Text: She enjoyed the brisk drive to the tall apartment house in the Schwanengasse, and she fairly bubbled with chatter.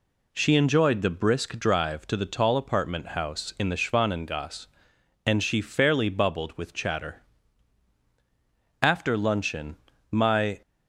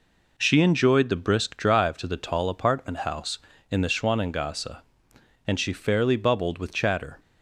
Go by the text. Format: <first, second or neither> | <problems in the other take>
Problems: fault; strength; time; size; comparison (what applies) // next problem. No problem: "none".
second | goes on to say "After luncheon my"; strong; from 8.8 s on; 1.8 s long